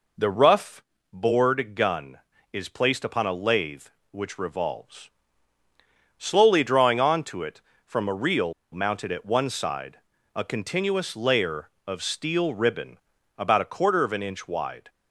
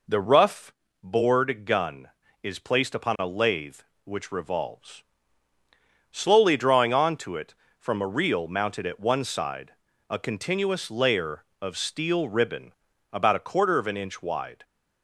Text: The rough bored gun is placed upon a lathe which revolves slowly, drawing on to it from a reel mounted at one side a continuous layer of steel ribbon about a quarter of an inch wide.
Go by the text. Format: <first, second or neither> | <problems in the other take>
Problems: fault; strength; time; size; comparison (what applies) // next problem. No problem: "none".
second | pauses between "rough" and "bored"; slight; at 0.8 s; 0.30 s long; slight in the second // pauses between "revolves" and "slowly"; at 5.0 s; 1.0 s long; also in the second // pauses between "reel" and "mounted"; slight; at 8.5 s; 0.19 s long // pauses between "side" and "a"; slight; at 9.9 s; 0.36 s long; slight in the second // pauses between "ribbon" and "about"; at 12.9 s; 0.42 s long; also in the second